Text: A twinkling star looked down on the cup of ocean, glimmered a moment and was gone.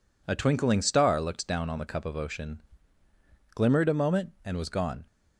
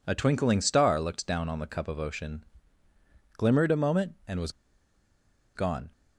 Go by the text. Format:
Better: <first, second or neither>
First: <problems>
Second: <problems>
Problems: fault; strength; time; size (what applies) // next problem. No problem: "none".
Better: first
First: none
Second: pauses between "was" and "gone"; at 4.5 s; 1.0 s long